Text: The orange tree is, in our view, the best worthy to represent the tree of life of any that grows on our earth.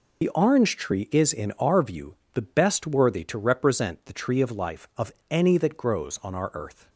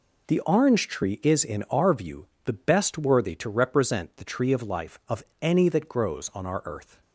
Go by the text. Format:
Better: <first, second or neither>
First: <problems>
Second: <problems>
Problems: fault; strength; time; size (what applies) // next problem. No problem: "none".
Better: second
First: loses the start of "The"; at 0.2 s; 60 ms // pauses between "of" and "any"; slight; at 5.1 s; 0.18 s long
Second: pauses between "of" and "any"; slight; at 5.2 s; 0.18 s long